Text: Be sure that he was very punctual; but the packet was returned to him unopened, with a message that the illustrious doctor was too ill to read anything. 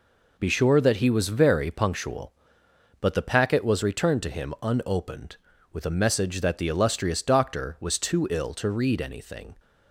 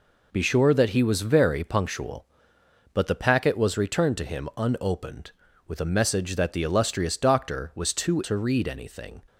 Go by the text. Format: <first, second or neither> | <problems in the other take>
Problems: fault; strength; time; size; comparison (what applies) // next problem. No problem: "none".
first | skips "ill"; at 8.2 s